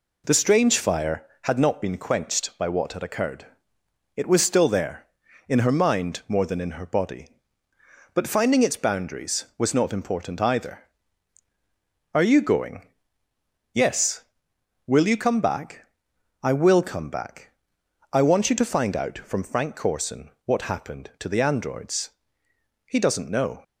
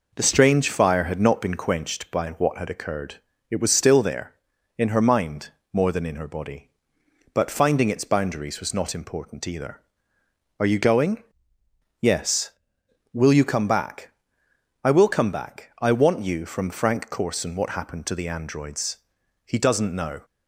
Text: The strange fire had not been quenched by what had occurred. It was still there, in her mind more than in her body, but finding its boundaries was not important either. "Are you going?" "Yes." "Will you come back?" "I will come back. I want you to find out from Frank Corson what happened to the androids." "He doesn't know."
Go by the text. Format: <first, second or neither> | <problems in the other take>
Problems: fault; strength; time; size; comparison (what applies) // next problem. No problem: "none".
first | pauses between "mind" and "more"; slight; at 5.5 s; 0.22 s long // skips "to find out"; at 16.4 s